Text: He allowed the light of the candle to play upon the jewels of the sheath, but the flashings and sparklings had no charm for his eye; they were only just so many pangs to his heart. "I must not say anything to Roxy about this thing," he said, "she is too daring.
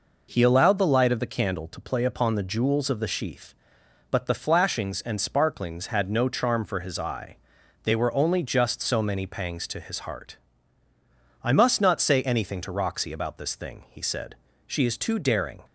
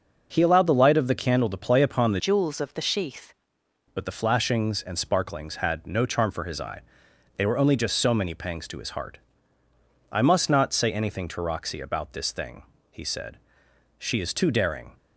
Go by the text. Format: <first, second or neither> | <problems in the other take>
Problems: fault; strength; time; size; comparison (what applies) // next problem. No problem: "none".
first | starts louder than the rest; until 1.3 s; 6 dB // changes voice from "jewels" to "sheath"; from 2.1 to 3.3 s; 1.2 s long